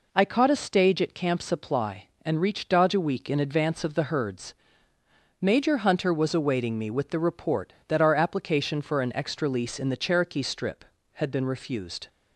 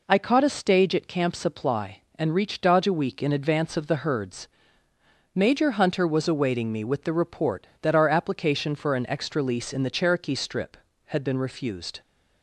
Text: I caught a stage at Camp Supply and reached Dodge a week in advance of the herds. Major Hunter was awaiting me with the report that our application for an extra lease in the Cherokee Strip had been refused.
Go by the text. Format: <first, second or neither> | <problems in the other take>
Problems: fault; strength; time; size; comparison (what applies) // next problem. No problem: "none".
neither | none